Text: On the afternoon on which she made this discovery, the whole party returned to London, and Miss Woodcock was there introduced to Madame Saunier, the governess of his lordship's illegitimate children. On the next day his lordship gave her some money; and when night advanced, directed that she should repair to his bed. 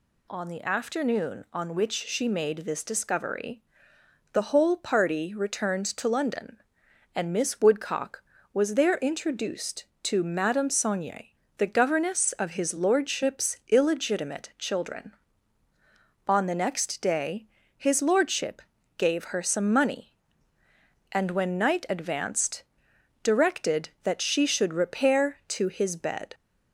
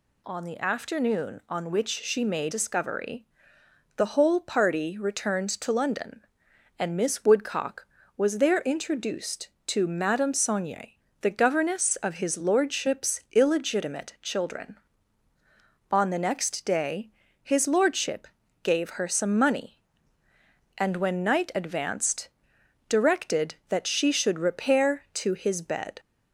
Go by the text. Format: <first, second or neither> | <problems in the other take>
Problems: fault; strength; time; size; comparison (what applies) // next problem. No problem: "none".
first | skips "this"; at 2.5 s // pauses between "day" and "his"; slight; at 17.0 s; 0.32 s long; slight in the first // pauses between "lordship" and "gave"; at 18.2 s; 0.38 s long; also in the first